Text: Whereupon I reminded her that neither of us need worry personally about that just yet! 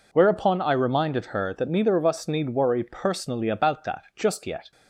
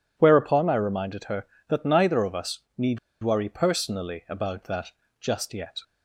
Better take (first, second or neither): first